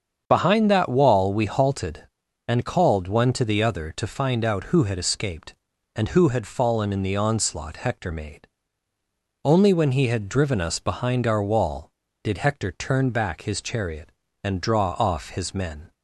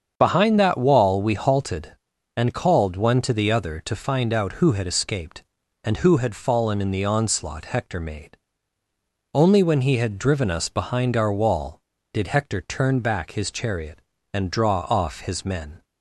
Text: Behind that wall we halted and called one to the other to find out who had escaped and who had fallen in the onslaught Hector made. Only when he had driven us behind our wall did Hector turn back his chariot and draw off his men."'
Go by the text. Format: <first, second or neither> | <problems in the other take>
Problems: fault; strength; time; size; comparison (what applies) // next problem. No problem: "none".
neither | starts louder than the rest; strong; the same in both